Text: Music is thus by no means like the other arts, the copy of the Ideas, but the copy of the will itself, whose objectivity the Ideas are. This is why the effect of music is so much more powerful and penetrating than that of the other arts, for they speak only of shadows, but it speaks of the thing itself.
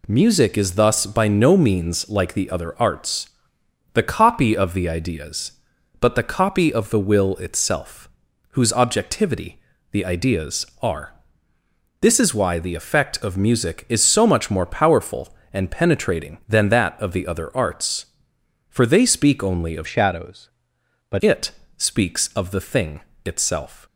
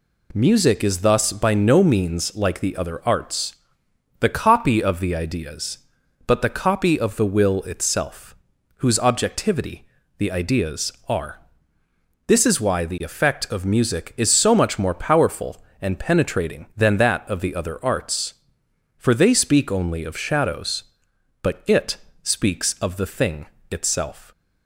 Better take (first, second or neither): second